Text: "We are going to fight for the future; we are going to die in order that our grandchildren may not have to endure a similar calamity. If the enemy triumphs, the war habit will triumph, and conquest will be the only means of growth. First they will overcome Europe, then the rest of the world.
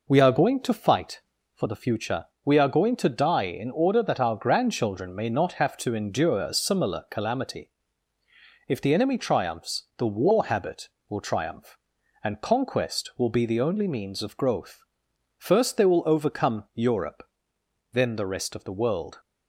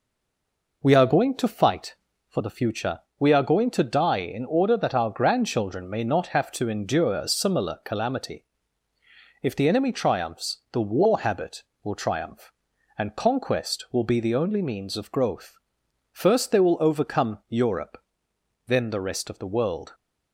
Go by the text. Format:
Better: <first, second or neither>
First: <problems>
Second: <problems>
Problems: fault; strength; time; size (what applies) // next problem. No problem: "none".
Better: first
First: none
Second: stays silent before the first word; slight; until 0.8 s; 0.8 s long